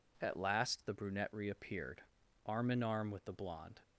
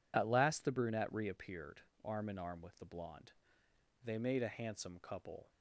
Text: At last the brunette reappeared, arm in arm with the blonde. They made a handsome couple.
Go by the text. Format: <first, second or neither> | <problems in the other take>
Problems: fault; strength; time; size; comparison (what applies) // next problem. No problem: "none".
second | stops before "They made a handsome couple"; at 3.8 s